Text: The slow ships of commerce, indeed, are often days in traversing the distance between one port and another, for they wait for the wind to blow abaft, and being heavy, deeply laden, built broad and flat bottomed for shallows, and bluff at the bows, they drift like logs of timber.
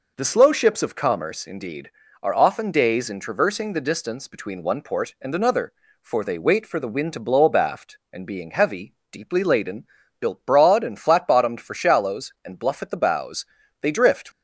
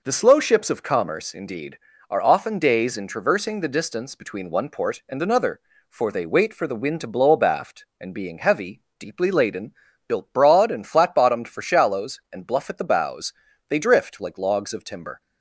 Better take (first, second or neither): second